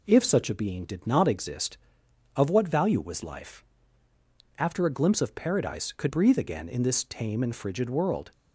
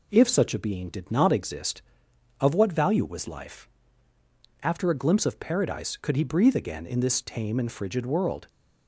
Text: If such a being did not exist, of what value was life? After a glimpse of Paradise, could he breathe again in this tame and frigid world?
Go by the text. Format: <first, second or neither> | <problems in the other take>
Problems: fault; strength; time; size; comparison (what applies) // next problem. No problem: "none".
second | skips "he"; at 6.0 s